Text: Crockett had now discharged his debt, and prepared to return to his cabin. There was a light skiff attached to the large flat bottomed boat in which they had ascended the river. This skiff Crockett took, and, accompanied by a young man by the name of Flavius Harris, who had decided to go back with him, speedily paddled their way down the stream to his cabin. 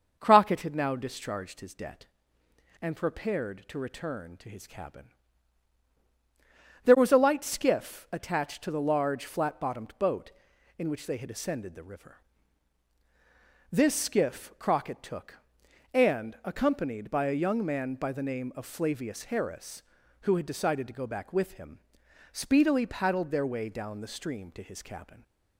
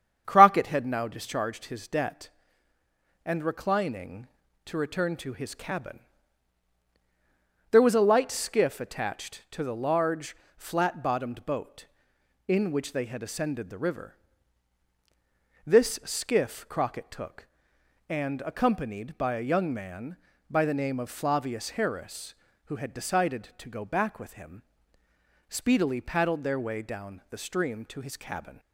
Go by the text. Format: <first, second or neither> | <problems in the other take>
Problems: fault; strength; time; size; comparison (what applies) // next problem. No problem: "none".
first | starts louder than the rest; strong; until 1.2 s; 8 dB // says "reclining" for "prepared"; at 3.4 s // pauses between "large" and "flat"; slight; at 10.3 s; 0.22 s long